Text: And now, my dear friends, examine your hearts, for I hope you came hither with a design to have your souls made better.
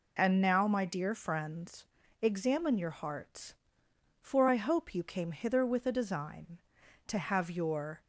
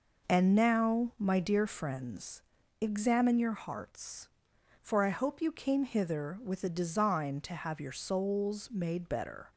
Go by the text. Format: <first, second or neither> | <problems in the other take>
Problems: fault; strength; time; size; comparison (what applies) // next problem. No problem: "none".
second | stops before "souls made better"; at 8.0 s